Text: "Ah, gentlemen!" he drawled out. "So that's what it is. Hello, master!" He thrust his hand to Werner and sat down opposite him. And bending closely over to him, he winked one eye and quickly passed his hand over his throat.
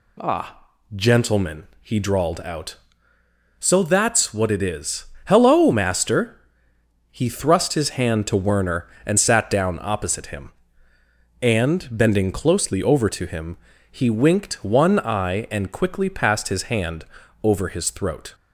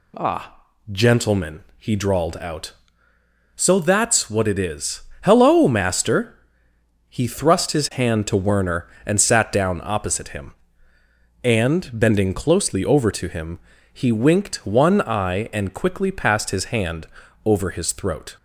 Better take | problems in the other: neither | pauses between "hand" and "over"; the same in both

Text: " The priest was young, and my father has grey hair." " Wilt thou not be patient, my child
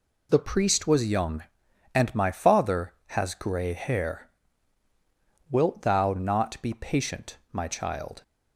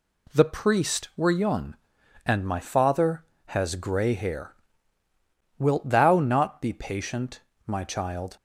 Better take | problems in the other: first | says "were" for "was"; at 1.1 s

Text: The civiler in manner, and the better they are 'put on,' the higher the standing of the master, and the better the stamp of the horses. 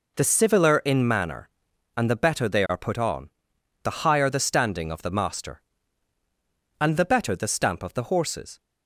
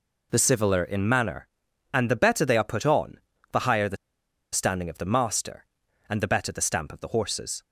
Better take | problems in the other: first | pauses between "the" and "standing"; noticeable; at 3.9 s; 0.56 s long

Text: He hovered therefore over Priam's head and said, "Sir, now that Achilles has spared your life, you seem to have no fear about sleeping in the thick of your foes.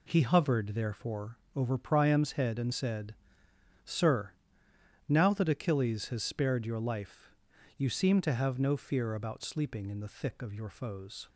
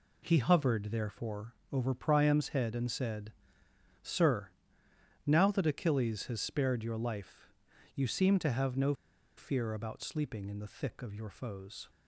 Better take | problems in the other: first | pauses between "therefore" and "over"; slight; at 1.5 s; 0.16 s long; slight in the first // pauses between "no" and "fear"; at 8.9 s; 0.43 s long

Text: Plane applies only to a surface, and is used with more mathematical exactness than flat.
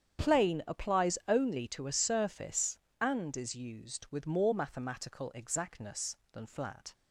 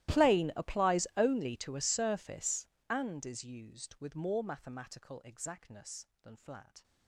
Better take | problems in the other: first | gets quieter; strong; throughout; 26.5 dB // starts louder than the rest; strong; until 1.2 s; 15 dB; strong in the first

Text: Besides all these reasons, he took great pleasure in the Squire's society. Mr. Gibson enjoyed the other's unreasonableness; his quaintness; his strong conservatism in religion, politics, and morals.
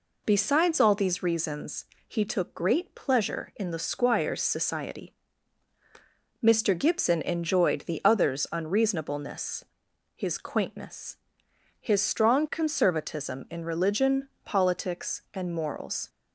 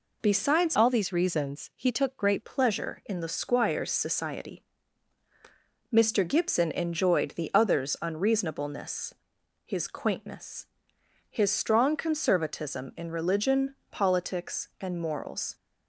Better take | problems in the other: first | changes voice from "all" to "great"; from 0.7 to 2.4 s; 1.7 s long

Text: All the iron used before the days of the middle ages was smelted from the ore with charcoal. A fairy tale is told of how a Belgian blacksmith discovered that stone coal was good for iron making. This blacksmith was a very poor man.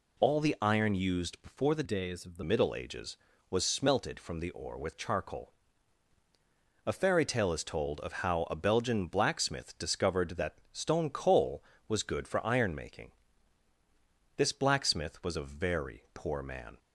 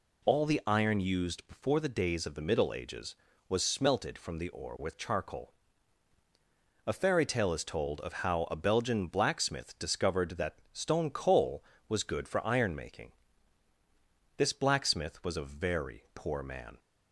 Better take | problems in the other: second | changes voice from "days" to "the"; from 1.8 to 2.4 s; 0.6 s long

